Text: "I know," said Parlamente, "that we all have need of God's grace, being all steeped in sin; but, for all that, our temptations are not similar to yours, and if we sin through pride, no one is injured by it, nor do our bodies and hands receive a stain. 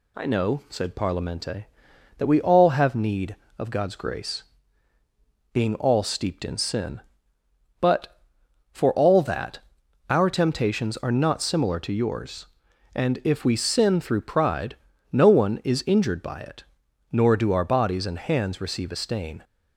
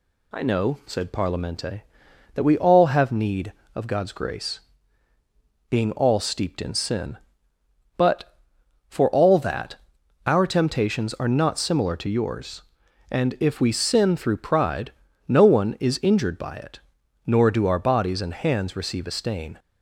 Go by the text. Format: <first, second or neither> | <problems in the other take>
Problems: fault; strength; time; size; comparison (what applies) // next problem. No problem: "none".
neither | none